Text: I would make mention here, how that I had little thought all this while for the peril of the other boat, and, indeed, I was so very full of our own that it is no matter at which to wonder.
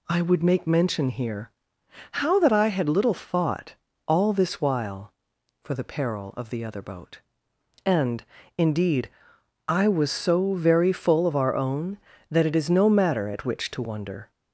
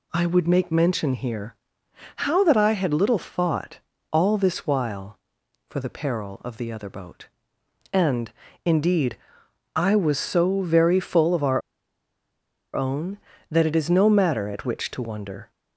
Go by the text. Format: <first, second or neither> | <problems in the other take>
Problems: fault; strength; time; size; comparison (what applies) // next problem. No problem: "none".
first | pauses between "thought" and "all"; slight; at 3.7 s; 0.32 s long; slight in the first // pauses between "our" and "own"; at 11.6 s; 1.1 s long